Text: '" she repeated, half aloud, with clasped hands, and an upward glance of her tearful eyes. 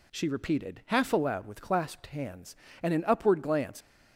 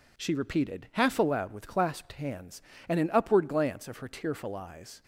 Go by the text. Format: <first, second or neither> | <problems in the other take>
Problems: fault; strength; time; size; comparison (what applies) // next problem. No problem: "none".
second | stops before "of her tearful eyes"; at 3.8 s